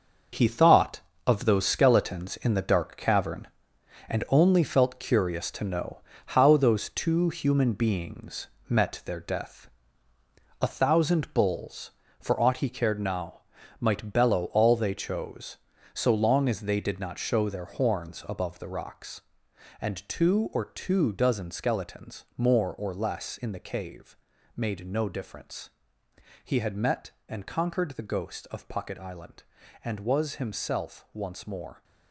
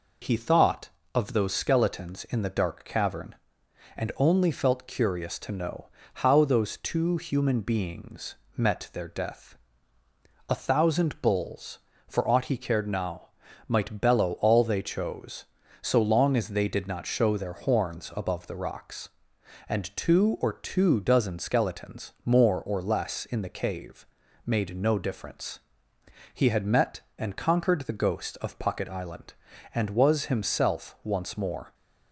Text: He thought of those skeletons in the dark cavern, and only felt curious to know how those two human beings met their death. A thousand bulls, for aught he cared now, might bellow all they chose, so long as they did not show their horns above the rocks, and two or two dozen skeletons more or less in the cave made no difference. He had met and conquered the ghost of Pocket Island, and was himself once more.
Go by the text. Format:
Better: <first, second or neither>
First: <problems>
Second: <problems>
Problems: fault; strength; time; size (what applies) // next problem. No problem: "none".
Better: second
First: gets quieter; strong; throughout; 9 dB // pauses between "know" and "how"; slight; at 5.9 s; 0.34 s long // pauses between "beings" and "met"; slight; at 8.4 s; 0.20 s long // pauses between "cave" and "made"; at 24.1 s; 0.40 s long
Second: pauses between "know" and "how"; slight; at 5.8 s; 0.34 s long // pauses between "beings" and "met"; slight; at 8.3 s; 0.20 s long // pauses between "cave" and "made"; at 24.0 s; 0.40 s long